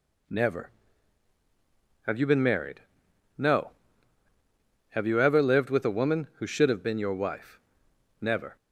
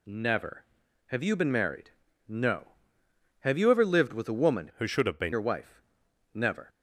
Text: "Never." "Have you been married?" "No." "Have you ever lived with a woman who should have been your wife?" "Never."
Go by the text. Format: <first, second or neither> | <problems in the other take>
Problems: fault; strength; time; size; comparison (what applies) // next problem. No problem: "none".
first | changes voice from "who" to "been"; from 4.7 to 5.3 s; 0.6 s long